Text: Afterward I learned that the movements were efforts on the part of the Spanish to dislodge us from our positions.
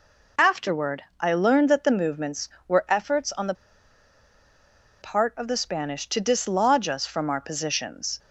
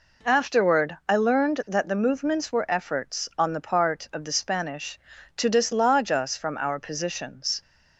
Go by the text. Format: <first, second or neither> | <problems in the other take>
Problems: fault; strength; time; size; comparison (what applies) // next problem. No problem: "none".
second | pauses between "Afterward" and "I"; slight; at 1.0 s; 0.18 s long // pauses between "the" and "part"; strong; at 3.5 s; 1.4 s long